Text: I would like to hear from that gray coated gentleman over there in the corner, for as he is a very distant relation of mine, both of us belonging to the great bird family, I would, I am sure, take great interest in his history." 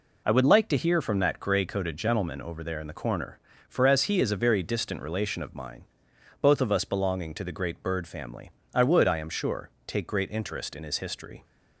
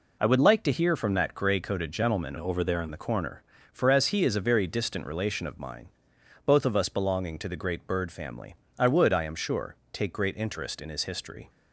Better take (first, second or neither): first